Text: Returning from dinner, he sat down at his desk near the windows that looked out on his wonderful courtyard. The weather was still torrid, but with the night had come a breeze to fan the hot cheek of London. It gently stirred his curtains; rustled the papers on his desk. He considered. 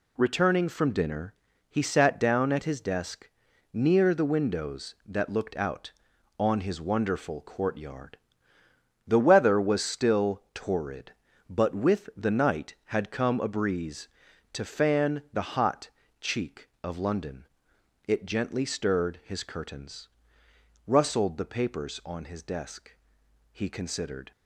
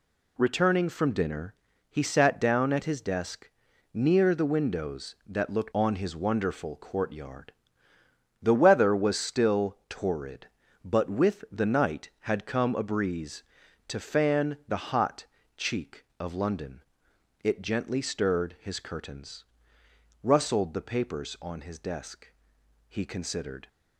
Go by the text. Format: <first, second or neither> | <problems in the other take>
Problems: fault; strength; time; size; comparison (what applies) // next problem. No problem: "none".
first | pauses between "desk" and "near"; at 3.4 s; 0.42 s long; also in the first // skips "out"; at 5.7 s // pauses between "hot" and "cheek"; slight; at 15.2 s; 0.32 s long; slight in the first